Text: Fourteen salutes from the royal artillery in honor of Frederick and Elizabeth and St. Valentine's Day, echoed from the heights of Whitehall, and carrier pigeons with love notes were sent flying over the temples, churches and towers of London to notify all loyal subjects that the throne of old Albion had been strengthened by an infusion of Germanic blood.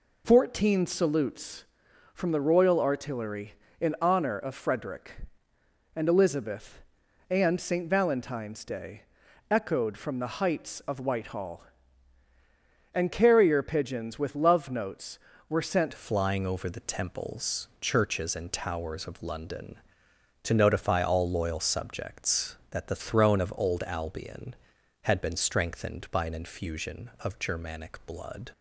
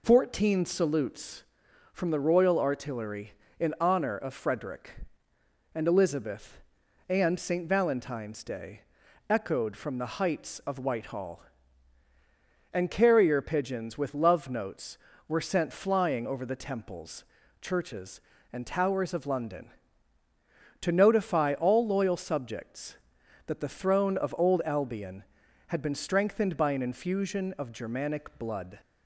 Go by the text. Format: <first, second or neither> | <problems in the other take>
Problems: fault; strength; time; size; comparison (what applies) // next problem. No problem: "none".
second | changes voice at "flying"; from 15.9 s on; 12.6 s long